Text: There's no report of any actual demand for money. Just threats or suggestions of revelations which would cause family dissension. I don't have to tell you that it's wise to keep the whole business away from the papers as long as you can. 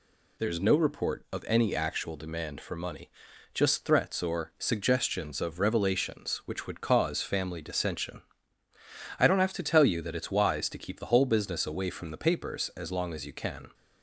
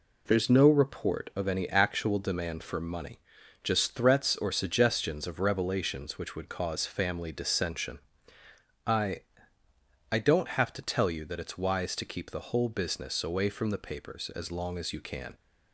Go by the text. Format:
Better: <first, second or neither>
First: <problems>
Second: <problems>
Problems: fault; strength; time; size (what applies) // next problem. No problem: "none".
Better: first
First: none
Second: says "I" twice; at 10.1 s